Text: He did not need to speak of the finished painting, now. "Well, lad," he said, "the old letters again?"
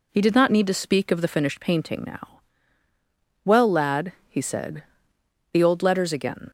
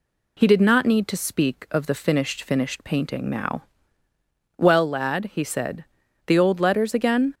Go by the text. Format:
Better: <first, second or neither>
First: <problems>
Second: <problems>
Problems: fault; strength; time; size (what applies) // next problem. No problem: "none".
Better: first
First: none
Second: says "finished" twice; at 2.4 s